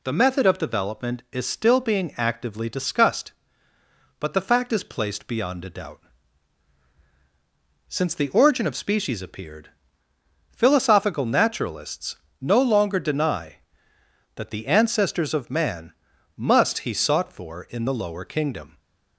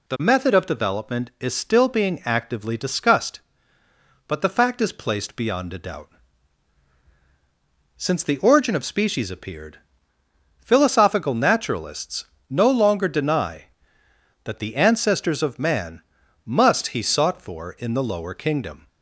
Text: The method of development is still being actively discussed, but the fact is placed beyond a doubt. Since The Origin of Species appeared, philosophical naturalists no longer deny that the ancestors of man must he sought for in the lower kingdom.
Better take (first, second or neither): neither